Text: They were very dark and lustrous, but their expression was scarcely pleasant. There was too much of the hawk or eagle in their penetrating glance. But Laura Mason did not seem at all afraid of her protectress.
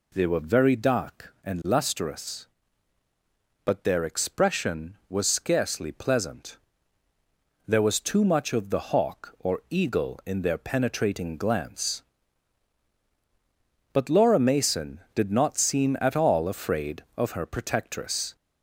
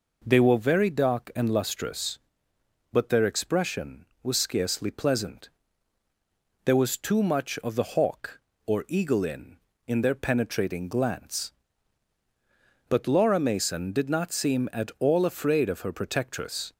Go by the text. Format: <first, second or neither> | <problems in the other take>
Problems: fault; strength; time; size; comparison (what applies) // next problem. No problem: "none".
first | says "in" twice; at 9.8 s